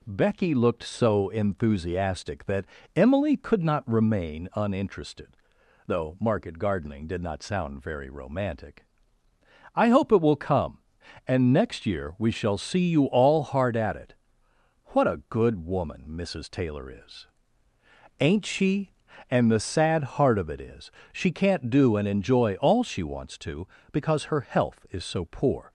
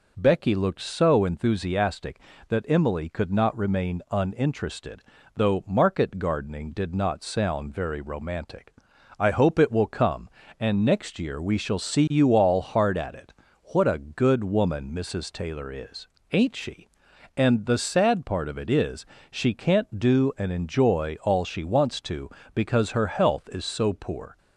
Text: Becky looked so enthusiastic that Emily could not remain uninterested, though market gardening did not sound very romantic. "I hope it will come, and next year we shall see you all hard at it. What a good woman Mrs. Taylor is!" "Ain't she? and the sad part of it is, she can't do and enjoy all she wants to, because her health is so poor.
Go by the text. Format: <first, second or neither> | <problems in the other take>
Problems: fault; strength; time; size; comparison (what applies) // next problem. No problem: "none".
second | pauses between "that" and "Emily"; slight; at 2.6 s; 0.32 s long // says "heart" for "part"; at 20.1 s